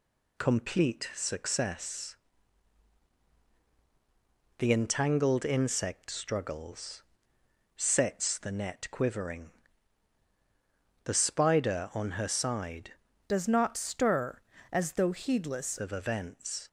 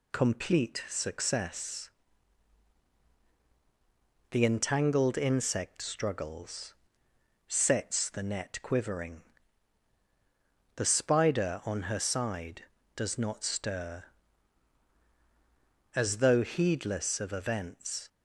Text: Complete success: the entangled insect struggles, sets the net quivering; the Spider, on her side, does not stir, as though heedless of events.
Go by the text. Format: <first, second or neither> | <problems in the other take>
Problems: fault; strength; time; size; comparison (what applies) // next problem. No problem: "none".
second | changes voice from "does" to "heedless"; from 13.2 to 15.7 s; 2.5 s long